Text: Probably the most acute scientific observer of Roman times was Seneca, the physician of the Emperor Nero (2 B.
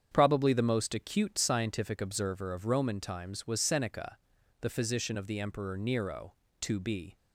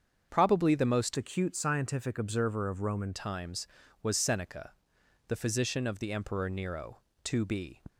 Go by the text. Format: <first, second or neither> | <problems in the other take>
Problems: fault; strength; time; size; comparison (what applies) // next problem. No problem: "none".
first | starts louder than the rest; strong; until 1.3 s; 7 dB; strong in the first // changes voice from "acute" to "Roman"; from 1.1 to 3.1 s; 2.0 s long